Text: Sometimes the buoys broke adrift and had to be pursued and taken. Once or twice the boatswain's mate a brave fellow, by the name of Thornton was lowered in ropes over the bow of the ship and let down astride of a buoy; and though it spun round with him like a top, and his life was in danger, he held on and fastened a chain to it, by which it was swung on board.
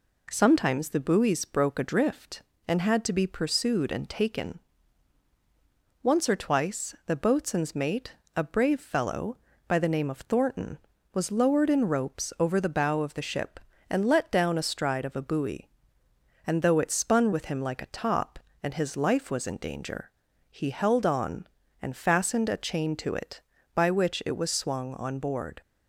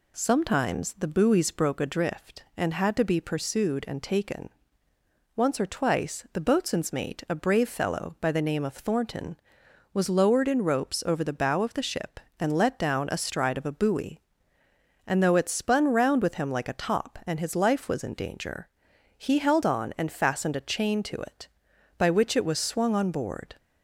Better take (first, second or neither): second